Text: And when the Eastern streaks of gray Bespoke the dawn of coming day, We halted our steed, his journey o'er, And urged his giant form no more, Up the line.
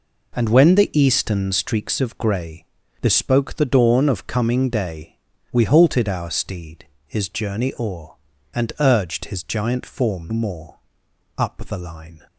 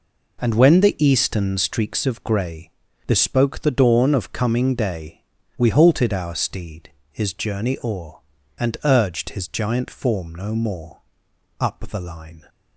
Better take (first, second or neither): second